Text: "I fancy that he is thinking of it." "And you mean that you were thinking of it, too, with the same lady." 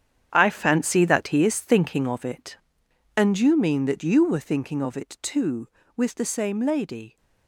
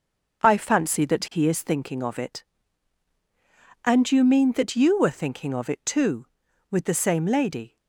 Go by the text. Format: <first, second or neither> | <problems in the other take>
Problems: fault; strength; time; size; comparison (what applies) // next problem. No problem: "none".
second | gets quieter; strong; throughout; 11 dB // starts louder than the rest; strong; until 1.3 s; 9 dB; noticeable in the second